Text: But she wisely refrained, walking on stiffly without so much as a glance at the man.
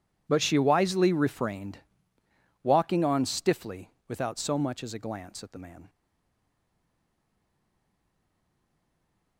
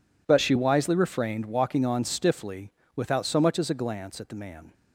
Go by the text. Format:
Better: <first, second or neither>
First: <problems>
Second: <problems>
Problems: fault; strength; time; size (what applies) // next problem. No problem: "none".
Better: second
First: pauses between "stiffly" and "without"; slight; at 3.9 s; 0.18 s long // stays silent after the last word; strong; from 5.8 s on; 3.5 s long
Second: pauses between "stiffly" and "without"; slight; at 2.7 s; 0.24 s long